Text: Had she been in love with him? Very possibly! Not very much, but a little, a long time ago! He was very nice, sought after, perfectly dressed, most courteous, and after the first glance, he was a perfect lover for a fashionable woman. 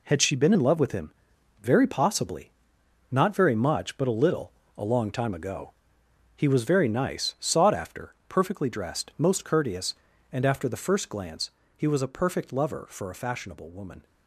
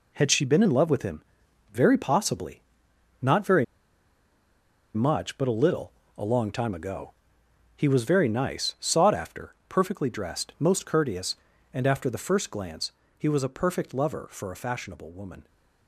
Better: first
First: none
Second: pauses between "very" and "much"; strong; at 3.6 s; 1.2 s long

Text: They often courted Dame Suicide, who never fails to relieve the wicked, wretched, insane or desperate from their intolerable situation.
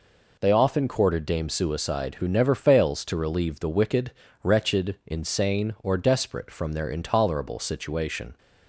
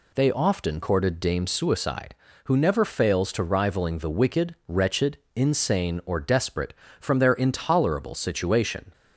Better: first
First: none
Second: says "rivaling" for "relieve"; at 3.4 s

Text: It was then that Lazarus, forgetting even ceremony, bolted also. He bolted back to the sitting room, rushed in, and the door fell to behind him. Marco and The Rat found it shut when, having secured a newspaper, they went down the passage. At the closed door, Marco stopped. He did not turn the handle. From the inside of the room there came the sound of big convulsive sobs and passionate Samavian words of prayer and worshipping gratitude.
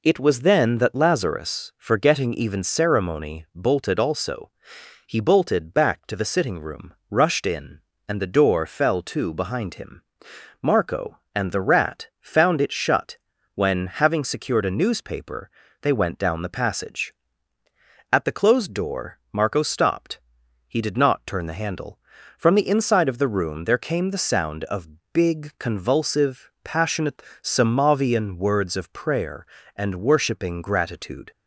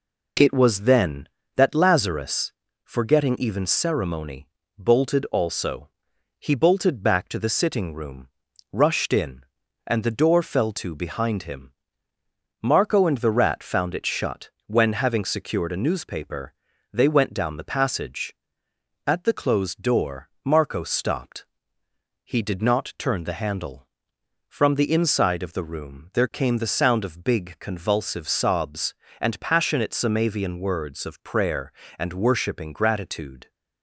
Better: second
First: pauses between "shut" and "when"; slight; at 13.1 s; 0.36 s long // pauses between "of" and "big"; slight; at 24.8 s; 0.24 s long // skips "sobs and"; at 26.5 s // pauses between "passionate" and "Samavian"; slight; at 27.2 s; 0.20 s long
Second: pauses between "shut" and "when"; slight; at 14.4 s; 0.18 s long

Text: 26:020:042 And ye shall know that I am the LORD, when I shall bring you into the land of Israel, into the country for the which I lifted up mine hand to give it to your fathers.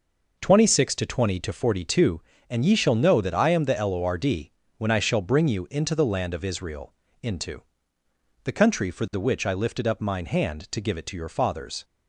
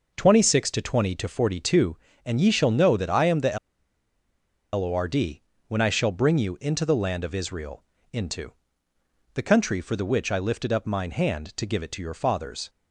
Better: first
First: pauses between "into" and "the"; noticeable; at 7.6 s; 0.80 s long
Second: pauses between "the" and "LORD"; at 3.5 s; 1.1 s long // pauses between "into" and "the"; noticeable; at 8.5 s; 0.80 s long

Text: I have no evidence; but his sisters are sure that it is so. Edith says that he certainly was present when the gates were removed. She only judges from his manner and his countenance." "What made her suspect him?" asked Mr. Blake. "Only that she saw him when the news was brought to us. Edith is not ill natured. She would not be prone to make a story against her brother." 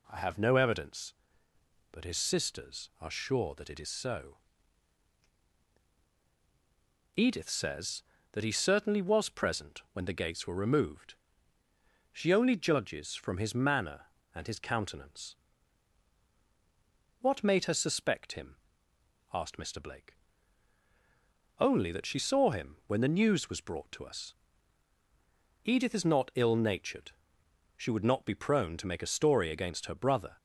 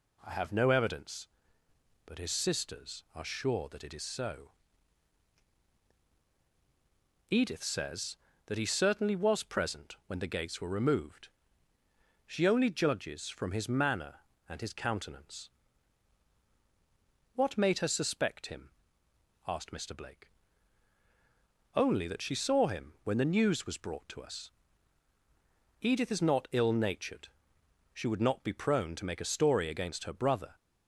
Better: neither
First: none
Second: none

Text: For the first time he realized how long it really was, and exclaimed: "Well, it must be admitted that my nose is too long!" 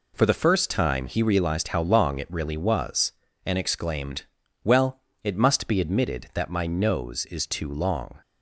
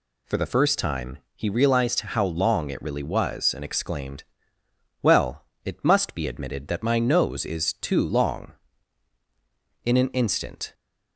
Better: first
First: none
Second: pauses between "time" and "he"; slight; at 1.1 s; 0.16 s long // goes on to say "In an instant"; noticeable; from 9.8 s on; 0.90 s long

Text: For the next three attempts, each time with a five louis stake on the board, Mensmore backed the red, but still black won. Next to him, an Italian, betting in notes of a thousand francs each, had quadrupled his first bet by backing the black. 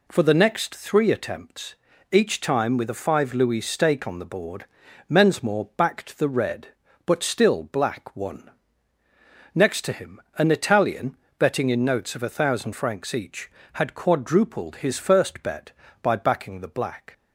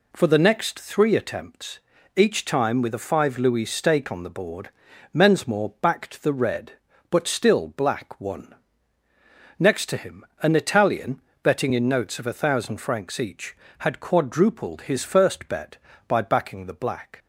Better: neither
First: none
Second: none

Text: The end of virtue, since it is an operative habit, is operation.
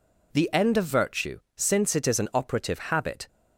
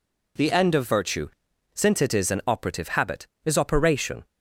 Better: second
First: stops before "is operation"; at 3.2 s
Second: none

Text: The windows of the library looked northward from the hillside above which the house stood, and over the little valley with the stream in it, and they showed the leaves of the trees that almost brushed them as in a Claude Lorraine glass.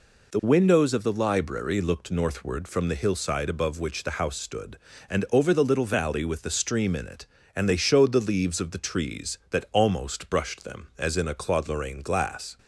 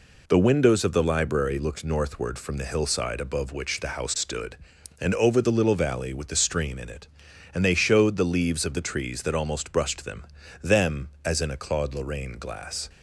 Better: first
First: none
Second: says "them" twice; at 10.6 s

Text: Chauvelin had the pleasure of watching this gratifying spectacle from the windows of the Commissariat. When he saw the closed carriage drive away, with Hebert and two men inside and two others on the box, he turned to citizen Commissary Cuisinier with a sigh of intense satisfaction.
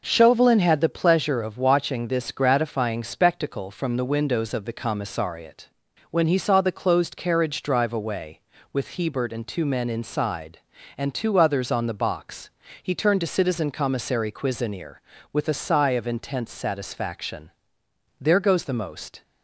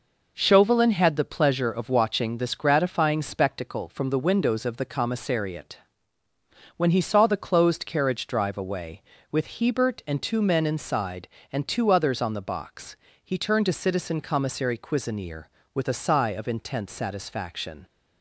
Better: second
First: goes on to say "There goes the most"; noticeable; from 18.2 s on; 1.0 s long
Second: none

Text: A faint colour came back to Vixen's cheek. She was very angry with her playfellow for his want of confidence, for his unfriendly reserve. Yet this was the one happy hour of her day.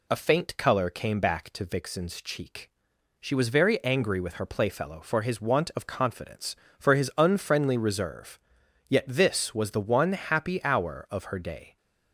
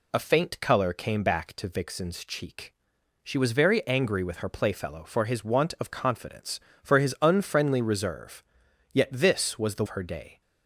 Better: first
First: none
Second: skips "one happy hour of"; at 9.8 s

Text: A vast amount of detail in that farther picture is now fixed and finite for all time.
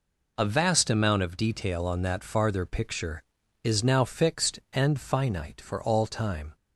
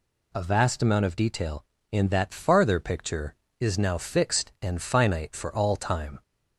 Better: second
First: says "on" for "in"; at 1.8 s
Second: none

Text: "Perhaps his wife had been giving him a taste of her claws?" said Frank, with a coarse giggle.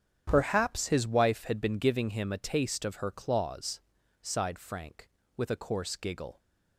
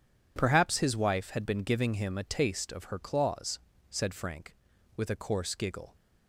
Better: second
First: starts louder than the rest; strong; until 1.2 s; 8 dB // says "sighed" for "said"; at 4.2 s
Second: none

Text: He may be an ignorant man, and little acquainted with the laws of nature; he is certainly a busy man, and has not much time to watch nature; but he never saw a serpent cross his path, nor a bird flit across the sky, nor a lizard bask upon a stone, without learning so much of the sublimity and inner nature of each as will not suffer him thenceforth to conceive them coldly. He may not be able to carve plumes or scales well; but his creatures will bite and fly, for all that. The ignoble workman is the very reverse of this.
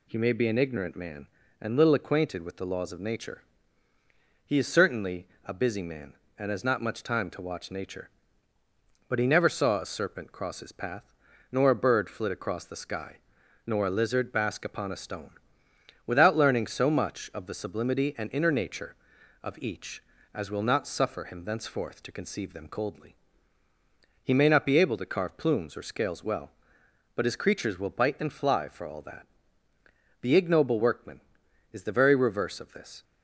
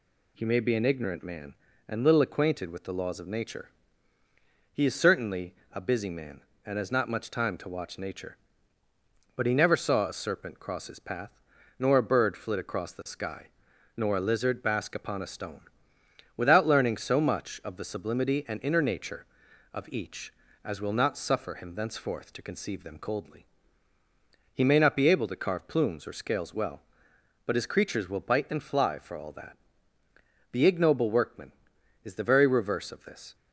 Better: neither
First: pauses between "certainly" and "a"; slight; at 5.2 s; 0.18 s long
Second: pauses between "certainly" and "a"; slight; at 5.5 s; 0.18 s long

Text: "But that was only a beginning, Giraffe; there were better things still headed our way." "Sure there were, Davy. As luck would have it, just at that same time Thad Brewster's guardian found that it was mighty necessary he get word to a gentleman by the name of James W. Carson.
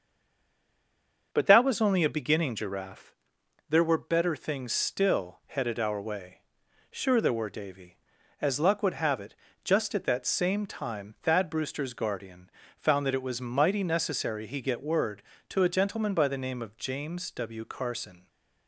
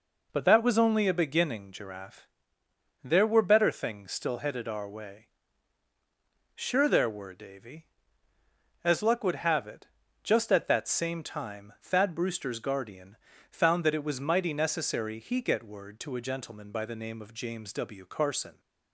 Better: second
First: stays silent before the first word; noticeable; until 1.3 s; 1.3 s long // starts louder than the rest; until 2.3 s; 6.5 dB // pauses between "guardian" and "found"; slight; at 12.5 s; 0.26 s long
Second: pauses between "guardian" and "found"; slight; at 13.1 s; 0.34 s long

